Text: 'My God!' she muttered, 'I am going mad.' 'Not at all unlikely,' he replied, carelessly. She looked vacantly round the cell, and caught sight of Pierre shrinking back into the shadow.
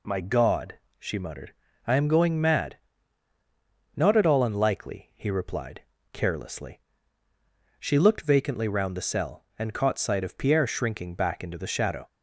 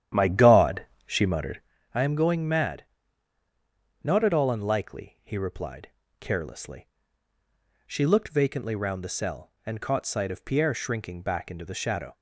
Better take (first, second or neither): first